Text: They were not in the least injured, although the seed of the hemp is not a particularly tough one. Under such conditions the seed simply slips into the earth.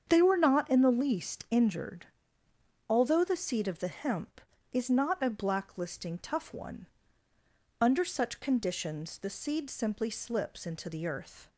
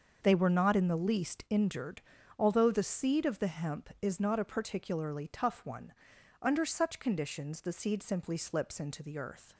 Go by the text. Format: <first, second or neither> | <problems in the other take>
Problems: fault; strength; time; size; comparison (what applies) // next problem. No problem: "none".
second | starts louder than the rest; strong; until 1.0 s; 7.5 dB; also in the second // says "blacklisting" for "particularly"; at 5.2 s